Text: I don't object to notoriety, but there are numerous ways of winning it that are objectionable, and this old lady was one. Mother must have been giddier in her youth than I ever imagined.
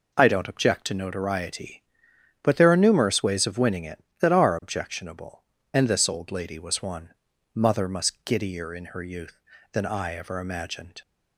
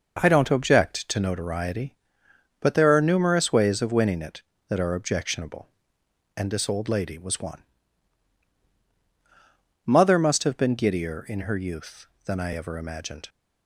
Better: second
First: skips "have been"; at 8.2 s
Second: none

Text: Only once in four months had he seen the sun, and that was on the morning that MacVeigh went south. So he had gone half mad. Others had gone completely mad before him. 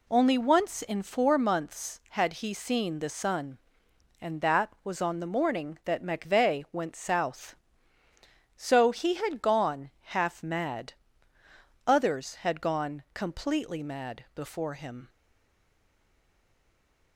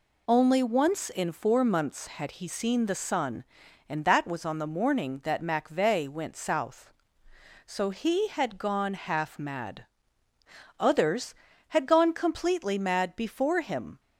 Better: second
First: stays silent after the last word; noticeable; from 15.0 s on; 2.1 s long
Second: none

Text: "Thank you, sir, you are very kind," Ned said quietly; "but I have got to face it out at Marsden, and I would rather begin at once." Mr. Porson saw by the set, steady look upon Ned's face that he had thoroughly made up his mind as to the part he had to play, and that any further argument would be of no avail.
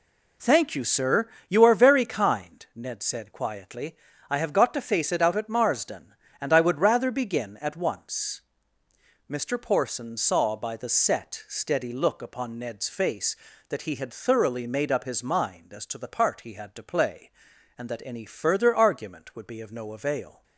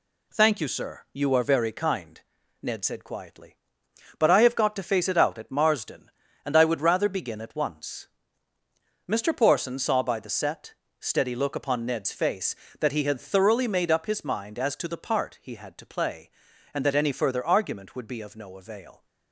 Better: second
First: skips "but"; at 4.1 s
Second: none

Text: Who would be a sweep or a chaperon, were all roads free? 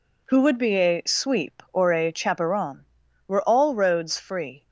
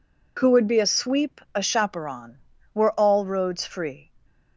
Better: first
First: none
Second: skips "or"; at 1.4 s

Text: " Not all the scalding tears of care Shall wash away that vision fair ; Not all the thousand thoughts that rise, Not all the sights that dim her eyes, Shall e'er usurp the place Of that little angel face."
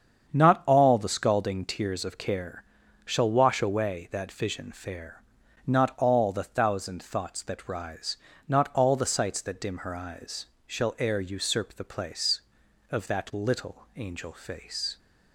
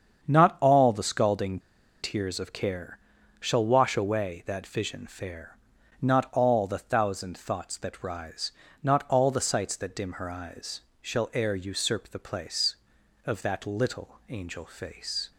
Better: first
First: starts louder than the rest; strong; until 1.3 s; 7.5 dB // pauses between "care" and "Shall"; at 2.6 s; 0.44 s long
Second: starts louder than the rest; strong; until 1.2 s; 7.5 dB // pauses between "scalding" and "tears"; at 1.5 s; 0.43 s long // pauses between "care" and "Shall"; at 2.9 s; 0.44 s long

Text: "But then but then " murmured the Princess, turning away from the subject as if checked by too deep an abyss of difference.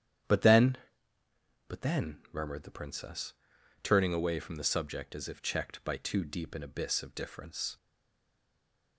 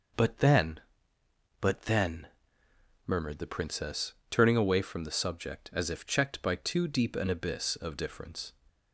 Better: second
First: starts louder than the rest; strong; until 2.1 s; 10 dB // stays silent after the last word; noticeable; from 7.7 s on; 1.2 s long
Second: none

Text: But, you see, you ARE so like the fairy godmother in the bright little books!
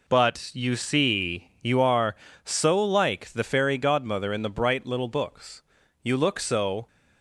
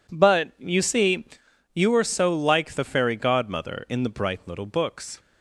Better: second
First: goes on to say "You look so"; noticeable; from 6.0 s on; 0.84 s long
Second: none

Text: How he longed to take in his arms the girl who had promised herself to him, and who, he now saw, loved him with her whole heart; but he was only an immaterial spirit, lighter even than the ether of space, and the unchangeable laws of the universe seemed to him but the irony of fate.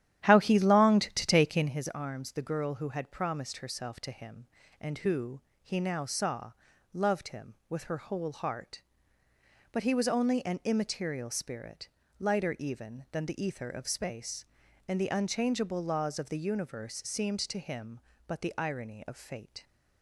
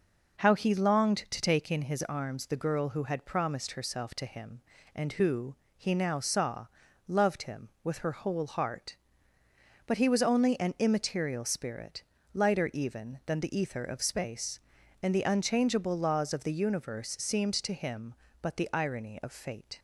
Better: second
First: starts louder than the rest; strong; until 1.8 s; 11.5 dB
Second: none

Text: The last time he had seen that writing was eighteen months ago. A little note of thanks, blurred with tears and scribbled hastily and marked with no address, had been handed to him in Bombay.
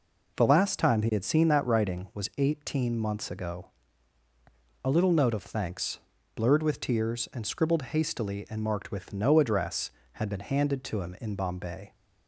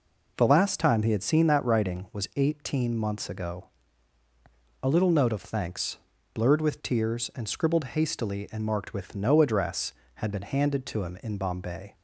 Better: neither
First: none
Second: none

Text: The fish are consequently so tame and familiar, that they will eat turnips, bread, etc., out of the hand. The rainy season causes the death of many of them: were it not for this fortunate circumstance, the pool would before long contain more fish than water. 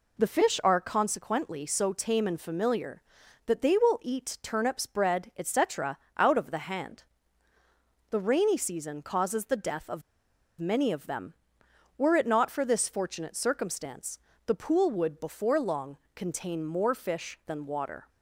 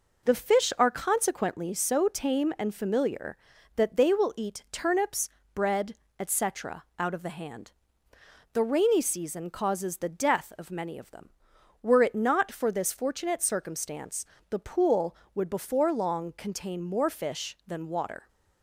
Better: second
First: pauses between "of" and "many"; noticeable; at 10.0 s; 0.56 s long // pauses between "long" and "contain"; slight; at 15.9 s; 0.20 s long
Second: none

